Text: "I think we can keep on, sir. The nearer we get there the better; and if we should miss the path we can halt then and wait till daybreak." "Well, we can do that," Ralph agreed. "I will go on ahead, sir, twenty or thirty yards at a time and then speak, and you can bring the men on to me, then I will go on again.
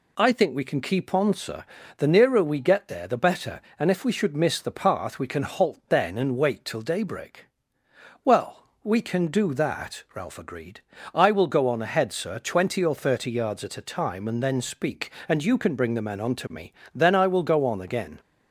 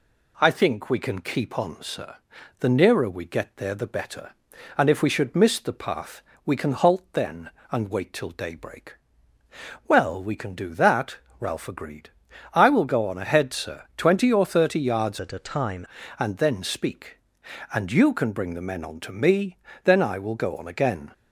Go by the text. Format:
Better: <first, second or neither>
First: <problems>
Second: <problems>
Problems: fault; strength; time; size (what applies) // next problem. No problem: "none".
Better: first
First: none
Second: pauses between "path" and "we"; slight; at 6.2 s; 0.22 s long // changes voice from "at" to "time"; from 15.1 to 15.8 s; 0.7 s long